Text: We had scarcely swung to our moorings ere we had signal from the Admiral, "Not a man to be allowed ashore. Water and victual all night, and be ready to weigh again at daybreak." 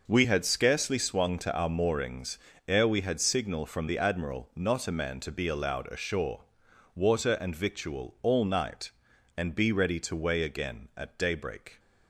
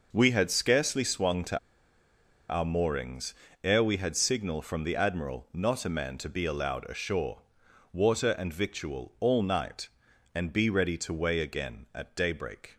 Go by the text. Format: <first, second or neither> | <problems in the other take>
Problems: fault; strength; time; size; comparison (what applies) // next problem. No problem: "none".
first | pauses between "to" and "our"; noticeable; at 1.5 s; 0.93 s long // pauses between "moorings" and "ere"; slight; at 3.3 s; 0.32 s long; slight in the first